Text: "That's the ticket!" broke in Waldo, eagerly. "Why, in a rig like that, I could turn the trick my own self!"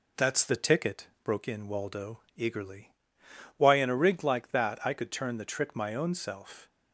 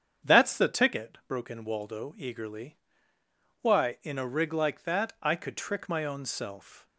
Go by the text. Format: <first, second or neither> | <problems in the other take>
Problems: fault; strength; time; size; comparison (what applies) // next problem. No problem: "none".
first | starts louder than the rest; strong; until 1.3 s; 8 dB // skips "turn the"; at 5.5 s